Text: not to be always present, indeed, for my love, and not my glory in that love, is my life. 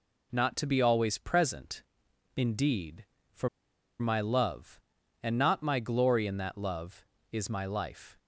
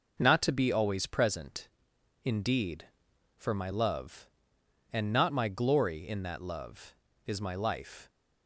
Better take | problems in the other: second | pauses between "for" and "my"; noticeable; at 3.4 s; 0.52 s long

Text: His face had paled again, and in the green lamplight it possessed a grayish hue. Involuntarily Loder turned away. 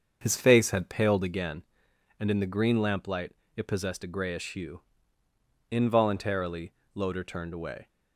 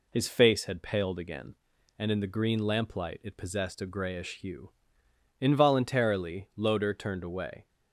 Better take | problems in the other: second | starts louder than the rest; until 1.5 s; 7 dB // pauses between "lamplight" and "it"; slight; at 3.3 s; 0.22 s long // pauses between "Involuntarily" and "Loder"; slight; at 6.7 s; 0.22 s long

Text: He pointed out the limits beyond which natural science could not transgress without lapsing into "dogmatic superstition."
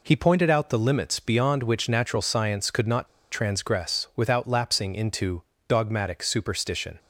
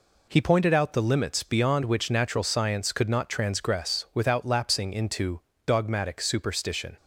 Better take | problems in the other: second | pauses between "not" and "transgress"; slight; at 3.0 s; 0.24 s long // pauses between "into" and "dogmatic"; slight; at 5.4 s; 0.26 s long; slight in the second

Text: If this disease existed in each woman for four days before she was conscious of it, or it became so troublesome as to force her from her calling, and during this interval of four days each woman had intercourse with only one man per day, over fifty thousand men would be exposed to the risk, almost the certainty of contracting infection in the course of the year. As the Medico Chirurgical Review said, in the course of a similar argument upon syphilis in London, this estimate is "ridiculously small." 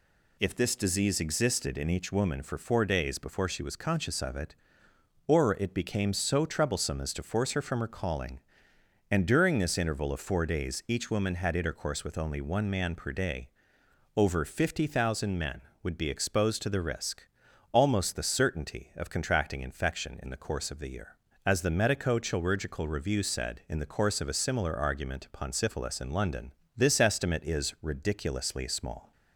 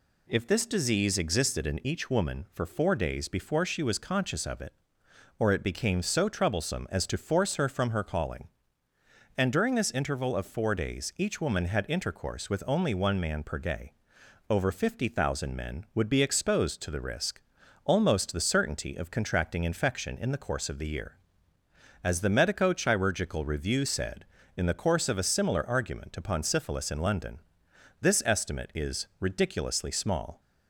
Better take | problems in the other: neither | none

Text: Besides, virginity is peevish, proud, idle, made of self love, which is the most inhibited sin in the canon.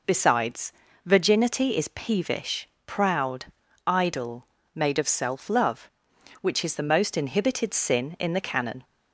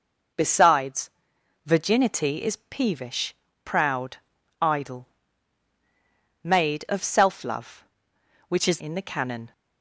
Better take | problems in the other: first | skips "the most inhibited sin"; at 8.7 s

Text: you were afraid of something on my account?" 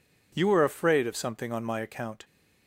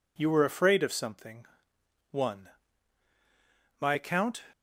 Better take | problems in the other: first | says "one" for "on"; at 2.1 s

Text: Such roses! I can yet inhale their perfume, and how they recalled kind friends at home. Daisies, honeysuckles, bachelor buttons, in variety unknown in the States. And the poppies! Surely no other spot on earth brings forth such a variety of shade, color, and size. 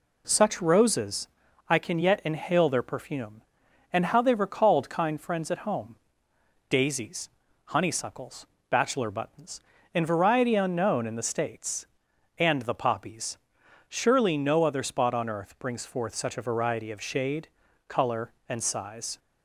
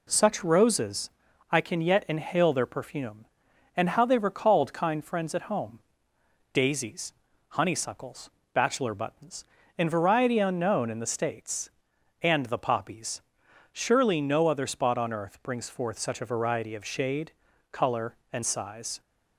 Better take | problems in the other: neither | none

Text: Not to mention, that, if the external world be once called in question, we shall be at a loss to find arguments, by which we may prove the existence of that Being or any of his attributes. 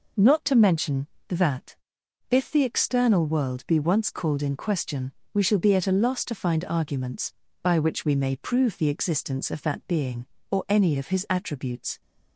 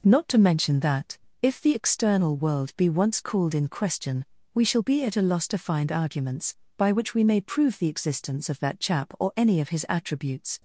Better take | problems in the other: first | says "Chap" for "Being"; at 8.7 s

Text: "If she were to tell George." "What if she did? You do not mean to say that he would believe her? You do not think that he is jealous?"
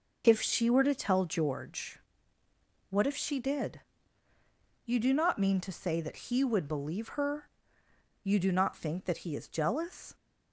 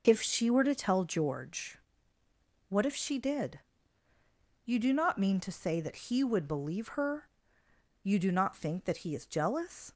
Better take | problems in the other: neither | none

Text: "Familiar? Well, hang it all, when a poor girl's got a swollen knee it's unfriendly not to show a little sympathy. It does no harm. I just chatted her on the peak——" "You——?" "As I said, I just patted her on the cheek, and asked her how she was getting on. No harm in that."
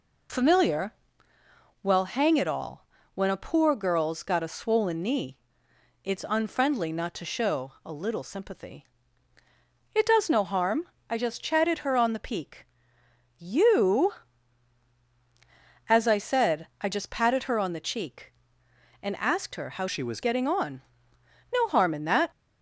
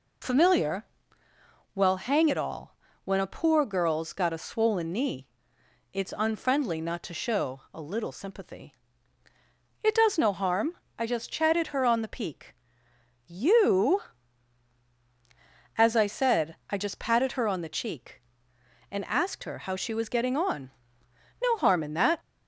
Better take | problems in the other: second | pauses between "knee" and "it's"; noticeable; at 5.3 s; 0.68 s long; noticeable in the second // changes voice from "she" to "was"; from 19.8 to 20.2 s; 0.4 s long

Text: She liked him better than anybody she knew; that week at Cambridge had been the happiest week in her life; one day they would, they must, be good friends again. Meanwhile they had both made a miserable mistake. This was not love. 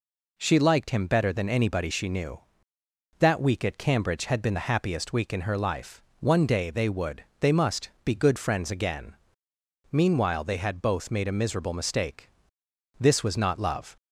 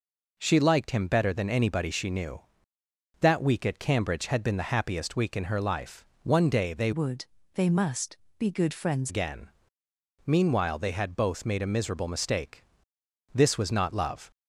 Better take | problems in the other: first | changes voice from "would" to "friends"; from 6.9 to 9.1 s; 2.2 s long

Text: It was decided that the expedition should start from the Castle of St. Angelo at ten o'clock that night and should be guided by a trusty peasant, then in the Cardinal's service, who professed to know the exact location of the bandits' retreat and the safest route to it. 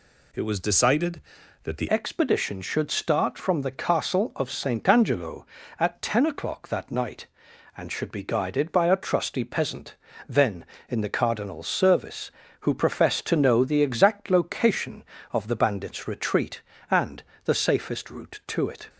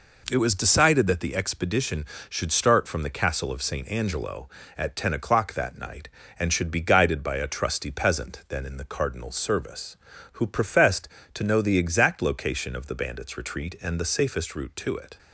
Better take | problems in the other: second | changes voice at "expedition"; from 1.9 s on; 16.9 s long // pauses between "and" and "the"; slight; at 17.2 s; 0.22 s long

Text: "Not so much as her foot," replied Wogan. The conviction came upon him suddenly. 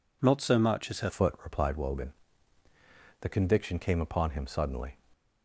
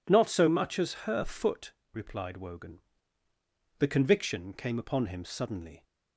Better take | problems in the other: second | changes voice at "foot"; from 1.0 s on; 3.9 s long

